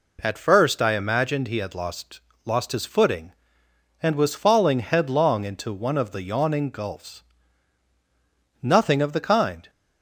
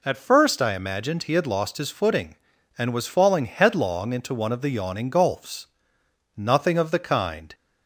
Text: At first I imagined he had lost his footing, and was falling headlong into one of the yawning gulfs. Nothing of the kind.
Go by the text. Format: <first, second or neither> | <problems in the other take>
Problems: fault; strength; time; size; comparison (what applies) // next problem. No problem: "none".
second | says "lost" twice; at 2.4 s